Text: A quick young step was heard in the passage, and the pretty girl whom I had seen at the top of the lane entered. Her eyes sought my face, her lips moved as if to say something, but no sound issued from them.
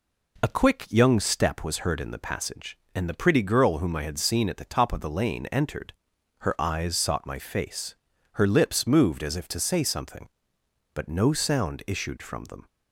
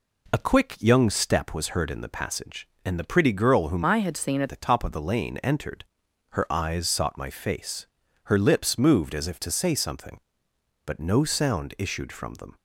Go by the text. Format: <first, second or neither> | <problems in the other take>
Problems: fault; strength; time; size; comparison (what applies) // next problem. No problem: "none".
first | changes voice from "I" to "at"; from 3.8 to 4.4 s; 0.6 s long